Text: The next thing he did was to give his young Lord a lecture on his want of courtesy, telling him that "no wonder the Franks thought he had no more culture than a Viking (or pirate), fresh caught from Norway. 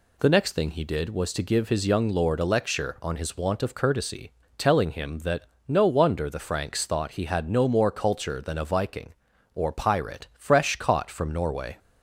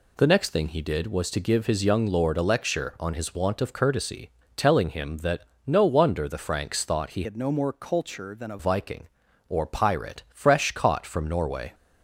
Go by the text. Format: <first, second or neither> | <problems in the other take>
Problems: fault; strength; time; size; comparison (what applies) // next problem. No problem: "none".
first | pauses between "that" and "no"; slight; at 5.4 s; 0.24 s long; slight in the first // changes voice from "had" to "a"; from 7.2 to 8.5 s; 1.3 s long